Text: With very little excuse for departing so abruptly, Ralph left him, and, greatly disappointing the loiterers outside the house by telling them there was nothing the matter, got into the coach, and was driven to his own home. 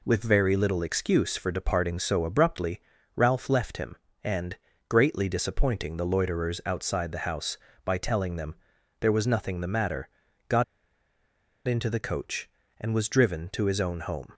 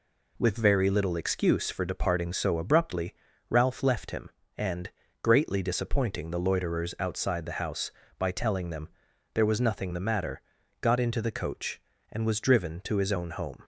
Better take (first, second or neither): second